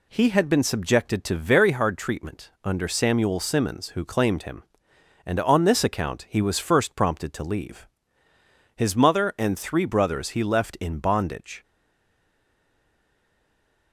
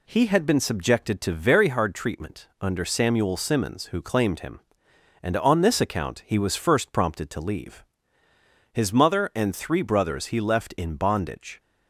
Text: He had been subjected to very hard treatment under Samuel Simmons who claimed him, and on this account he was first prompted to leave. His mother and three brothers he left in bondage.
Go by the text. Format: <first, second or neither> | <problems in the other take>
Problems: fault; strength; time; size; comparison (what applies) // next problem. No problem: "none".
second | stays silent after the last word; from 11.6 s on; 2.3 s long